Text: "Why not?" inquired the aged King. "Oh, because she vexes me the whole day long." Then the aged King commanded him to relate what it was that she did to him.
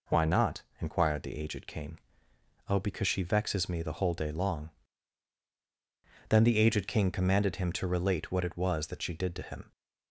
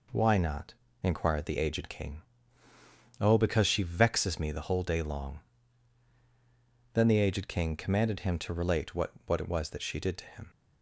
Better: first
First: none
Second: says "what" twice; at 9.2 s

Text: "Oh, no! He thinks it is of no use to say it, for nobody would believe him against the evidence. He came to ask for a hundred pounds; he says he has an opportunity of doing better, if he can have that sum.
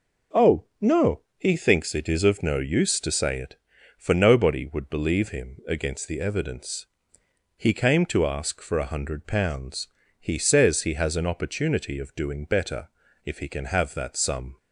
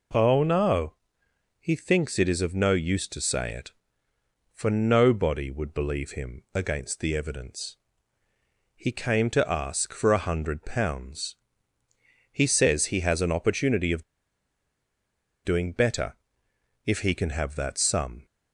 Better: first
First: none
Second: pauses between "of" and "doing"; strong; at 14.0 s; 1.4 s long

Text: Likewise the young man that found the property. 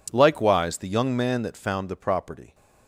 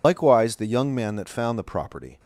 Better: first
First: none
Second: loses the start of "Likewise"; at 0.0 s; 65 ms

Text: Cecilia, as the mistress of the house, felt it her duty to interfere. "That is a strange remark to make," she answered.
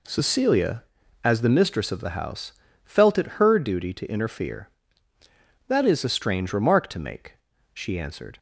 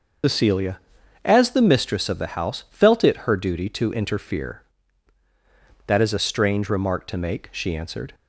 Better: first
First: none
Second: loses the start of "Cecilia"; at 0.2 s; 115 ms // starts louder than the rest; noticeable; until 1.7 s; 6 dB

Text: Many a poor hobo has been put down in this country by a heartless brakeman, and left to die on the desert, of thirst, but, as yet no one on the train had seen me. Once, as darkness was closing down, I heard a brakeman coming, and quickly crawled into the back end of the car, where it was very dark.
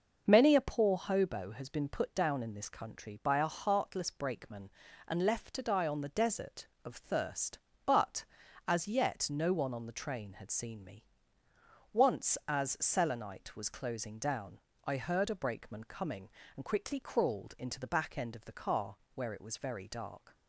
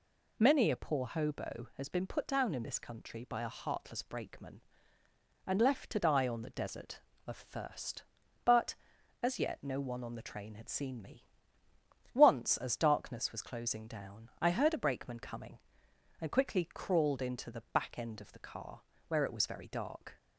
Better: second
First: says "selenite" for "darkness"; at 12.7 s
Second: none

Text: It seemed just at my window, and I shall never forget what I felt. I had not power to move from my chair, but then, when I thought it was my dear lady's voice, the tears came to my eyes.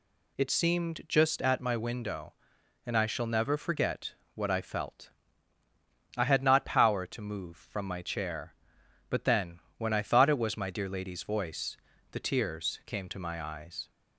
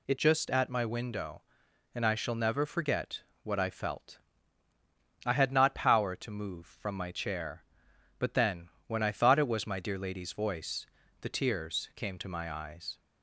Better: first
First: pauses between "forget" and "what"; slight; at 4.1 s; 0.20 s long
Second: skips "seemed"; at 0.1 s // pauses between "forget" and "what"; slight; at 3.2 s; 0.20 s long

